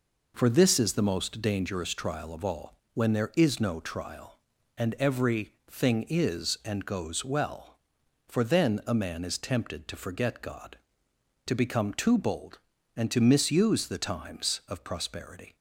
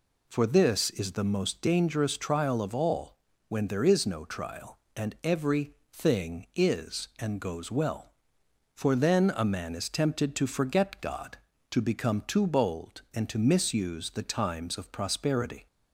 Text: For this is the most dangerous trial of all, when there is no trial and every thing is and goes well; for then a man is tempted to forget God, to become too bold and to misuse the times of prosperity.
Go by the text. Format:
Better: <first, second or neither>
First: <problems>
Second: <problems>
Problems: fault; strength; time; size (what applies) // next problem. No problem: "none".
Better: neither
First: pauses between "every" and "thing"; slight; at 5.5 s; 0.18 s long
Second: pauses between "every" and "thing"; slight; at 5.7 s; 0.18 s long